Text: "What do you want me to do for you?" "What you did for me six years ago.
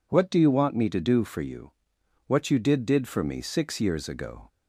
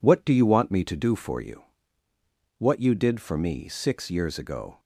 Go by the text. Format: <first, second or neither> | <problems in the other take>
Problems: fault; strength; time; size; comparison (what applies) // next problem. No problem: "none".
second | says "did" twice; at 2.8 s